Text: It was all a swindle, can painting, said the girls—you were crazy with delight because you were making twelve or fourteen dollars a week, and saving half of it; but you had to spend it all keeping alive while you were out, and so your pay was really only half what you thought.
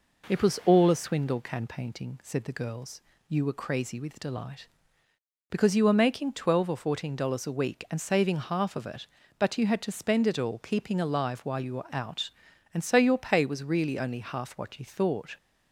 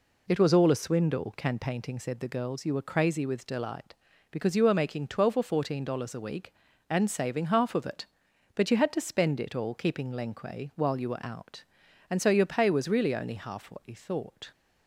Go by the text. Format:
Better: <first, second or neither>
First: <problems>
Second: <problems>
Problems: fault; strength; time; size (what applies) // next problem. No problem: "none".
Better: first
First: none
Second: says "lenque" for "alive"; at 10.1 s